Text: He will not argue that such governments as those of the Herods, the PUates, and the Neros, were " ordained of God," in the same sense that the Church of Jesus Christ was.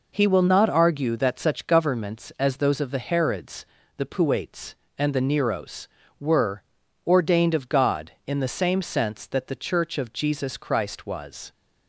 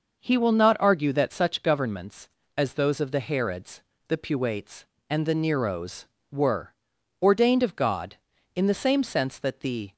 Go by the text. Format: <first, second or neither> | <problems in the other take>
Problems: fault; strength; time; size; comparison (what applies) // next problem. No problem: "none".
first | starts louder than the rest; noticeable; until 1.2 s; 6 dB // stops before "Church of Jesus Christ was"; at 9.9 s